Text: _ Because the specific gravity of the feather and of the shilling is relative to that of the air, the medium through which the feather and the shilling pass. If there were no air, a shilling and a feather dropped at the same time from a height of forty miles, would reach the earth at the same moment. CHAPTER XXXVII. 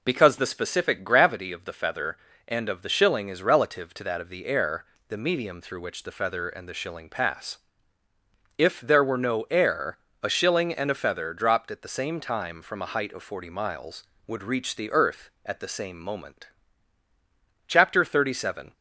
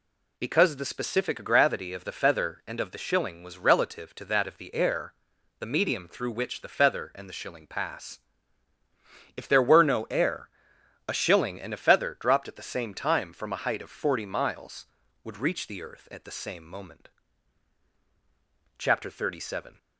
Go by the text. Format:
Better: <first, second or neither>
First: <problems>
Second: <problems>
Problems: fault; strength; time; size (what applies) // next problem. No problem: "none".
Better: first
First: none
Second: says "was" for "is"; at 3.4 s